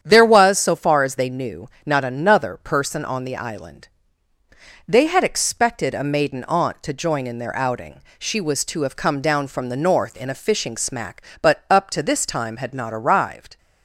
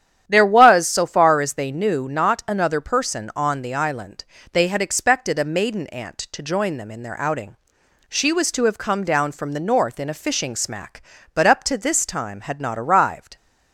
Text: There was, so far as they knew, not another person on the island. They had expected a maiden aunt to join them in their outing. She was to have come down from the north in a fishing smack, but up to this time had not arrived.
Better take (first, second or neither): second